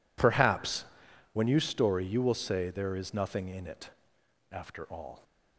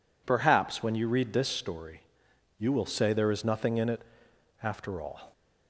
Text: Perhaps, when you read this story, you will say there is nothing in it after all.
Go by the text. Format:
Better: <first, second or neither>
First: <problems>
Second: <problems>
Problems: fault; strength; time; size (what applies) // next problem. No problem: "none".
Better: second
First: skips "read this"; at 1.6 s // pauses between "it" and "after"; noticeable; at 3.8 s; 0.62 s long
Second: pauses between "it" and "after"; noticeable; at 4.0 s; 0.60 s long